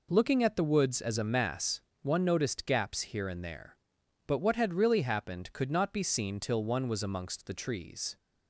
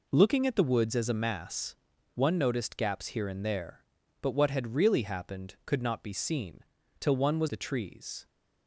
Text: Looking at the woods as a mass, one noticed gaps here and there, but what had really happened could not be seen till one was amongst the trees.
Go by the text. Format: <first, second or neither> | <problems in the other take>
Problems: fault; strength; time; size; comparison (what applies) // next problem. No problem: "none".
first | pauses between "seen" and "till"; at 6.6 s; 0.40 s long // skips "amongst"; at 7.4 s